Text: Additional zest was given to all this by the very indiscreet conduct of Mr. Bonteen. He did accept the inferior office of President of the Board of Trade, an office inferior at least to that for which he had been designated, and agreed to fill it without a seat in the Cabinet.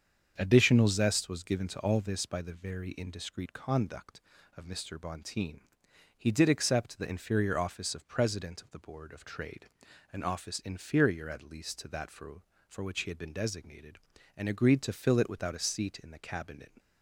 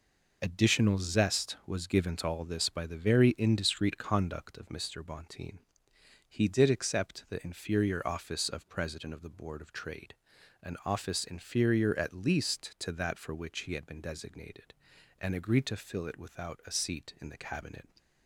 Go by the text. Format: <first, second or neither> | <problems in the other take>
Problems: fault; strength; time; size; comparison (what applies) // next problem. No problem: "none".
second | starts louder than the rest; strong; until 1.3 s; 7 dB // says "for" twice; at 12.6 s